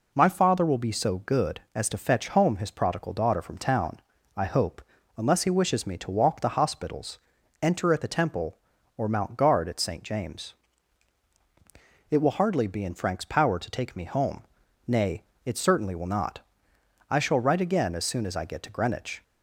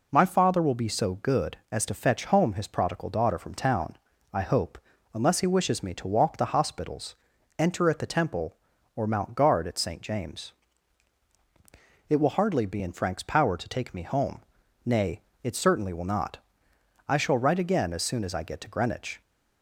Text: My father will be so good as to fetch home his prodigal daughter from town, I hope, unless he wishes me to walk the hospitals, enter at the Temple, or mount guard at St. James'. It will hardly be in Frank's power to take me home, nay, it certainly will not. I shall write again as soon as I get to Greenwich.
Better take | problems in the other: neither | none

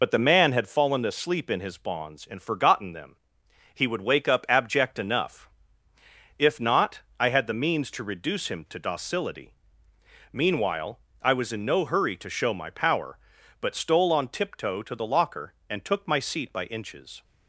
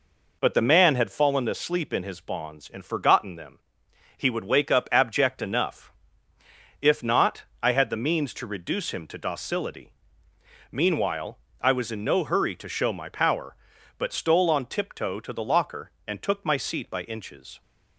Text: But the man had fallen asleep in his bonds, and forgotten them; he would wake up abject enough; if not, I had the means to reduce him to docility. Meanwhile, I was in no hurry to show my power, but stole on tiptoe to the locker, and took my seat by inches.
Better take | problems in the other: second | loses the start of "But"; at 0.0 s; 40 ms

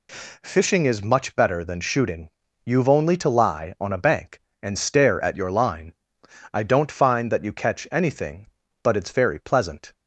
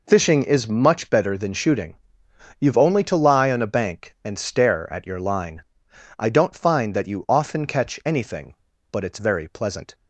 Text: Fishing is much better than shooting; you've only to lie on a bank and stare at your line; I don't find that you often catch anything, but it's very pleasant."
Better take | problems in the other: second | skips "often"; at 7.5 s

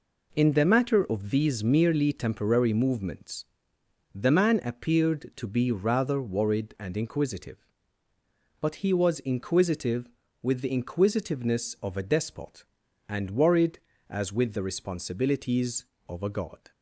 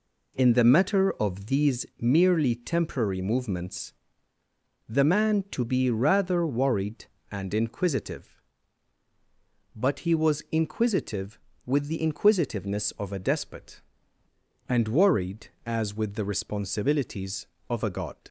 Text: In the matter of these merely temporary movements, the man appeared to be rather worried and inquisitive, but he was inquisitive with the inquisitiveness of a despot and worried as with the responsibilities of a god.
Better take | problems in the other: first | skips "appeared"; at 5.4 s

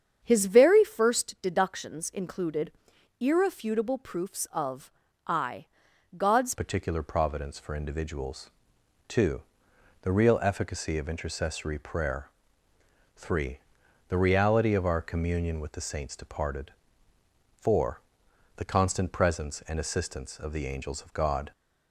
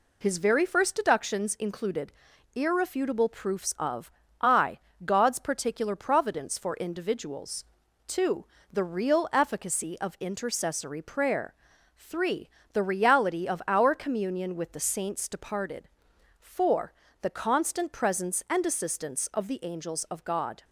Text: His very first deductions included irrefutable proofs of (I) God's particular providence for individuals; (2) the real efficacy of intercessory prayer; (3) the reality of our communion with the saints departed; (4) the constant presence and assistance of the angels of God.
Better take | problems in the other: second | starts louder than the rest; strong; until 1.2 s; 8 dB // pauses between "included" and "irrefutable"; noticeable; at 2.7 s; 0.48 s long; also in the second // pauses between "of" and "I"; at 4.8 s; 0.38 s long; slight in the second // changes voice at "particular"; from 6.5 s on; 15.0 s long

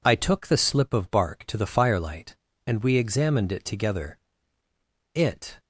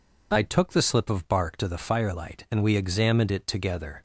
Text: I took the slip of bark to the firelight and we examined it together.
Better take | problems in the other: second | goes on to say "It"; slight; from 5.1 s on; 0.46 s long

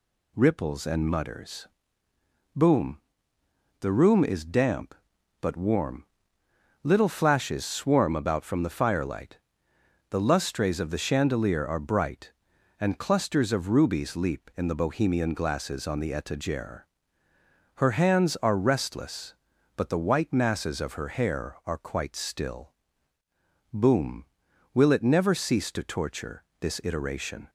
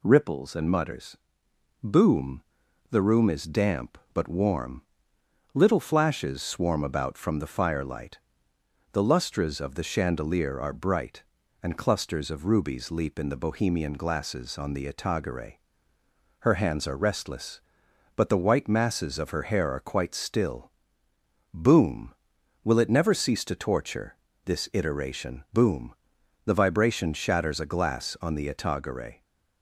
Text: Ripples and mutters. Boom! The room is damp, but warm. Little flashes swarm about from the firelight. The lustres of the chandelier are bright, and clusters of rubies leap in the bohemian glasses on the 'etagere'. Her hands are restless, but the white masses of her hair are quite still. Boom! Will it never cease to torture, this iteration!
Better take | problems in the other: first | goes on to say "Boom The vibration shatters a glass on the etagere"; strong; from 25.5 s on; 3.7 s long

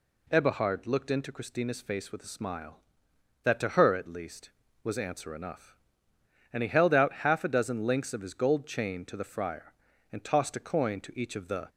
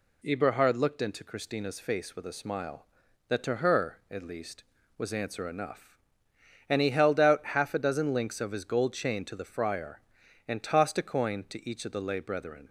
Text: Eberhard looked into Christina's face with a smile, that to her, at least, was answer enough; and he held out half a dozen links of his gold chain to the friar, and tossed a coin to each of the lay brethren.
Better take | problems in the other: second | stops before "lay brethren"; at 11.6 s

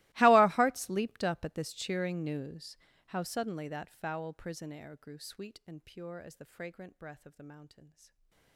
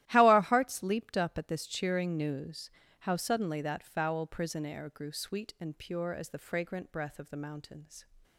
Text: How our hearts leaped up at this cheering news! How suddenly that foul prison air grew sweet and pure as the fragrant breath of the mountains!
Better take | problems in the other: second | gets quieter; strong; throughout; 26 dB // starts louder than the rest; strong; until 1.1 s; 20.5 dB; strong in the second // stays silent after the last word; slight; from 7.8 s on; 0.7 s long

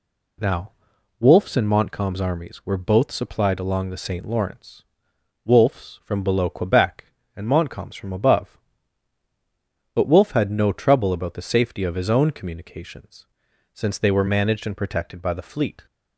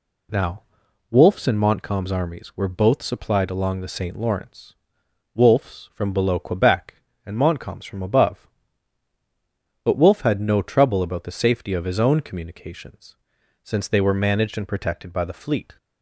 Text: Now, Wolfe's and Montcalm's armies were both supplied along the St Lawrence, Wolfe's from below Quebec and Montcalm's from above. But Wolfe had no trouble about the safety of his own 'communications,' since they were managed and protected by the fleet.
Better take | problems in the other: neither | none

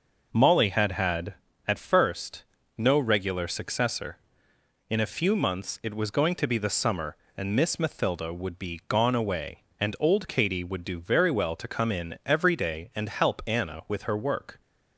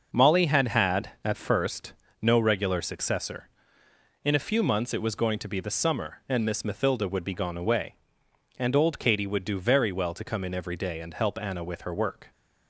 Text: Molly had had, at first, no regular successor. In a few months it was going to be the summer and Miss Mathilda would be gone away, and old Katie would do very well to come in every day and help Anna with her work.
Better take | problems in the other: neither | none

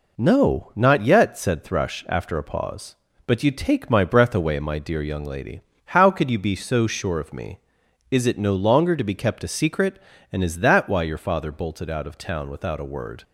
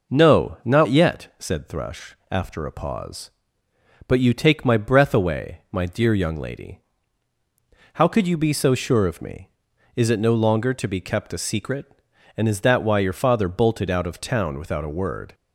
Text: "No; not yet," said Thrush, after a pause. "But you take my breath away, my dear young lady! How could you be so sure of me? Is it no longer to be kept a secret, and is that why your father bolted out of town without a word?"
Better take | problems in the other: neither | none

